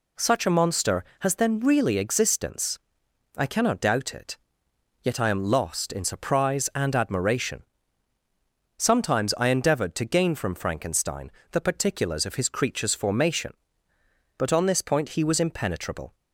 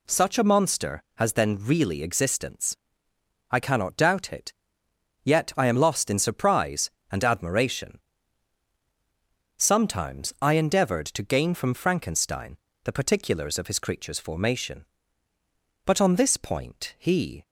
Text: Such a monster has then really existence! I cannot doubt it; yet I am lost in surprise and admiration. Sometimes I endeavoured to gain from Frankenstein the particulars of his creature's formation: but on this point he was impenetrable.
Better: first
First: pauses between "Frankenstein" and "the"; slight; at 11.3 s; 0.20 s long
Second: pauses between "Frankenstein" and "the"; slight; at 12.5 s; 0.26 s long // stops before "was impenetrable"; at 17.4 s

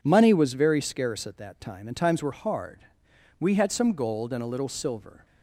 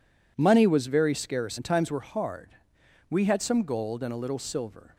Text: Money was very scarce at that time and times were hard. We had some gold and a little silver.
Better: first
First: none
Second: skips "at that time"; at 1.5 s

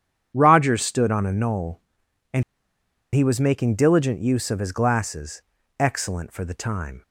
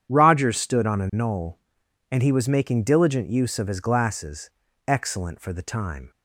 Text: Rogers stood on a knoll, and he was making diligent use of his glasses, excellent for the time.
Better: second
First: starts louder than the rest; strong; until 1.3 s; 9 dB // pauses between "and" and "he"; noticeable; at 2.4 s; 0.71 s long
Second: starts louder than the rest; strong; until 1.1 s; 9 dB

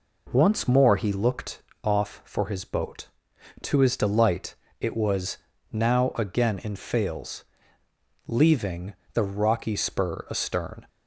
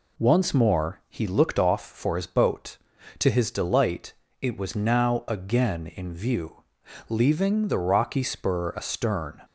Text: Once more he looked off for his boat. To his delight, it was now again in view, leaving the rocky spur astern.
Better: second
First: pauses between "looked" and "off"; slight; at 1.6 s; 0.20 s long // pauses between "was" and "now"; slight; at 5.3 s; 0.34 s long // says "fails" for "view"; at 6.7 s // pauses between "leaving" and "the"; slight; at 8.9 s; 0.22 s long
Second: none

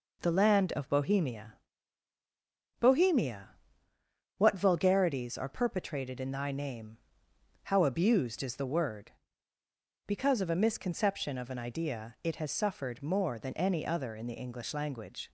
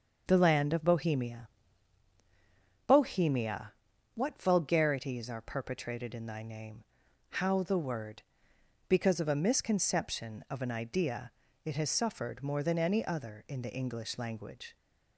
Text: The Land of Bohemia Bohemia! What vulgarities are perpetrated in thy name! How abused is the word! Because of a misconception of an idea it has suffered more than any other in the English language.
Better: first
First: pauses between "Bohemia" and "Bohemia"; strong; at 1.5 s; 1.2 s long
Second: starts louder than the rest; until 1.2 s; 6.5 dB // pauses between "Bohemia" and "Bohemia"; strong; at 1.4 s; 1.4 s long // skips "abused is"; at 7.6 s // pauses between "idea" and "it"; slight; at 11.3 s; 0.34 s long

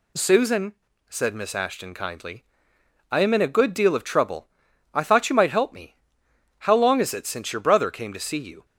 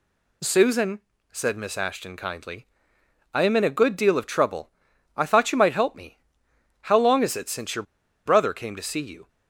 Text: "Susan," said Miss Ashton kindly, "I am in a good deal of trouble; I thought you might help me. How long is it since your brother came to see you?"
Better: first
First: none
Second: pauses between "your" and "brother"; at 7.8 s; 0.42 s long

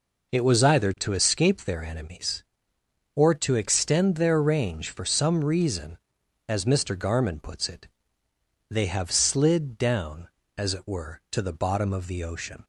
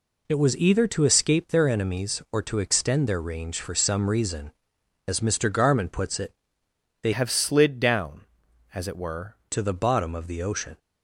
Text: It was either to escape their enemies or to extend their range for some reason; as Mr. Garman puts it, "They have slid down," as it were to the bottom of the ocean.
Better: first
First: none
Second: changes voice from "have" to "were"; from 7.1 to 9.3 s; 2.2 s long

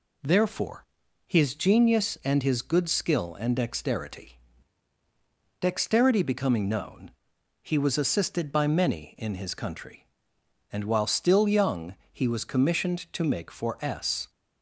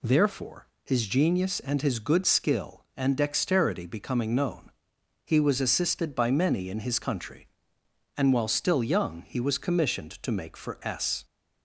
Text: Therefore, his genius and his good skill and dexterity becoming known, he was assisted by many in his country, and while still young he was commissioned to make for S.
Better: second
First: says "dexterity" twice; at 5.6 s // pauses between "young" and "he"; slight; at 11.9 s; 0.18 s long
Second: none

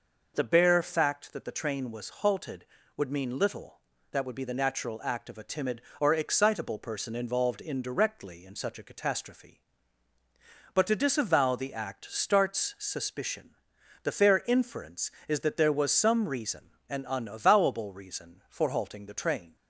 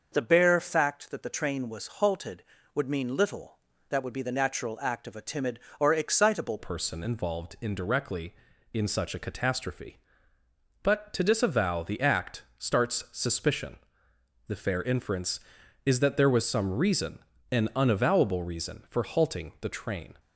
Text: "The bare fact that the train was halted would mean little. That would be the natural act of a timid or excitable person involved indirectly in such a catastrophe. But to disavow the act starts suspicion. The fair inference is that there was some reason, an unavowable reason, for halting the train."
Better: first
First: none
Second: starts louder than the rest; until 1.1 s; 6.5 dB // changes voice at "person"; from 6.5 s on; 13.6 s long

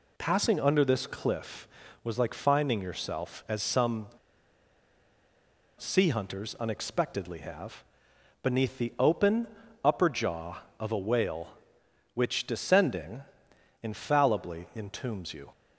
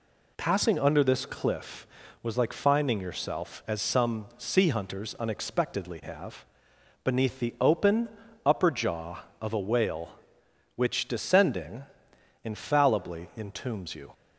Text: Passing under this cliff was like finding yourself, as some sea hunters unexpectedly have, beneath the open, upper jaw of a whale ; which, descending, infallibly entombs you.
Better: second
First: pauses between "some" and "sea"; strong; at 4.0 s; 1.6 s long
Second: none

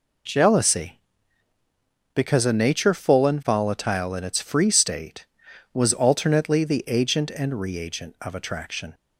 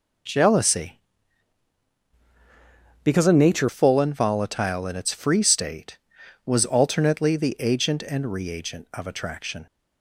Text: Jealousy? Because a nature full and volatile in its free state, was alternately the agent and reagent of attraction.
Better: first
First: none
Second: changes voice from "Because" to "nature"; from 3.0 to 3.6 s; 0.6 s long

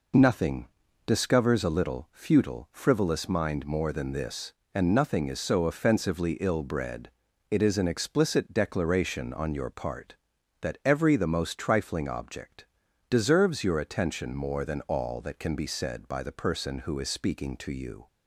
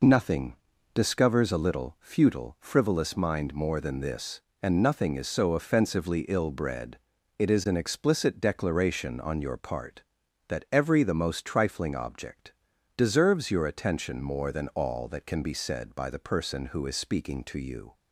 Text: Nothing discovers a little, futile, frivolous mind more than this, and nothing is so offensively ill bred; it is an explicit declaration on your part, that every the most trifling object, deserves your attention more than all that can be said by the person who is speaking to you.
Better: neither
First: pauses between "Nothing" and "discovers"; at 0.6 s; 0.38 s long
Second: pauses between "Nothing" and "discovers"; at 0.5 s; 0.38 s long

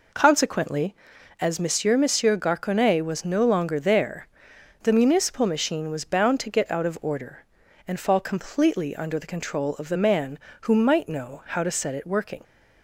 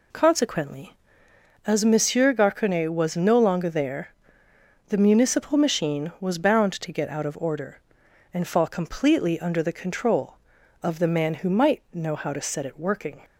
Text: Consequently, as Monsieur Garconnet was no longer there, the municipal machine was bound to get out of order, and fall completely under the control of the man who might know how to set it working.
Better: second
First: says "Monsieur" twice; at 1.9 s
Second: none

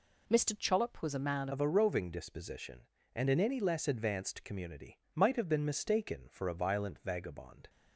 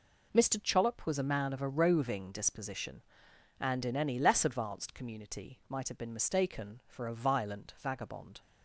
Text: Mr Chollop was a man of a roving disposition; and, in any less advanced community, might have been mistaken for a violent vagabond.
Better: second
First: changes voice at "of"; from 1.5 s on; 6.1 s long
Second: none

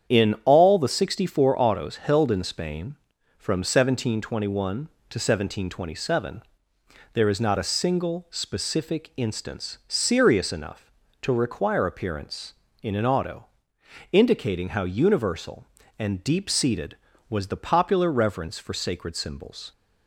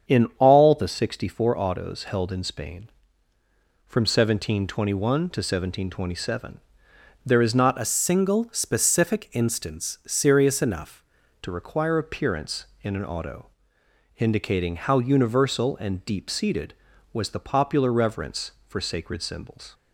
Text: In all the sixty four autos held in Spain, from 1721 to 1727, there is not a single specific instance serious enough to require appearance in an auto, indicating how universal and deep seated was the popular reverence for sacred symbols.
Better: first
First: starts louder than the rest; strong; until 1.1 s; 8.5 dB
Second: starts louder than the rest; strong; until 1.1 s; 7.5 dB // changes voice from "a" to "enough"; from 7.8 to 11.0 s; 3.2 s long

